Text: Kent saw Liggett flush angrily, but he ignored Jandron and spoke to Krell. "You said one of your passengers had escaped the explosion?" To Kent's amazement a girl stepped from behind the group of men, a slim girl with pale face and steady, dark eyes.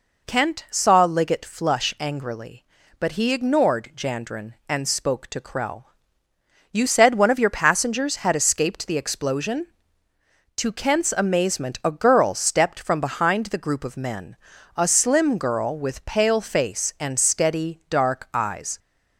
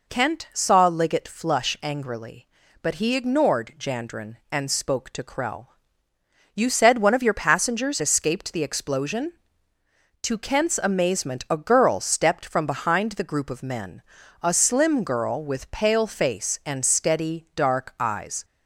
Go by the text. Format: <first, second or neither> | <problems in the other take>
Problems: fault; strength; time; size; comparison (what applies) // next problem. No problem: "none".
first | skips "had"; at 8.0 s